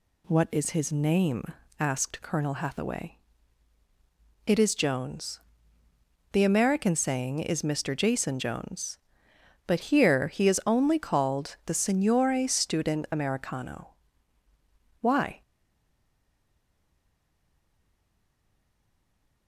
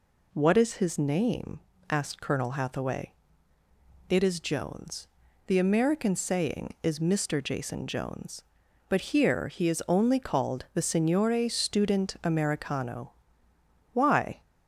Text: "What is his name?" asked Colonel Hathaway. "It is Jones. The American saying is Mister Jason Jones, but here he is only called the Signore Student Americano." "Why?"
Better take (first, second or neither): second